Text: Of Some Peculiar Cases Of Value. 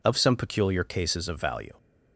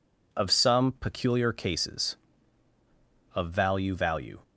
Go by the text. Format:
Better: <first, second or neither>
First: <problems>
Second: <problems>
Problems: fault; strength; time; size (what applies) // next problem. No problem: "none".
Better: first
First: none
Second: says "Value" twice; at 3.9 s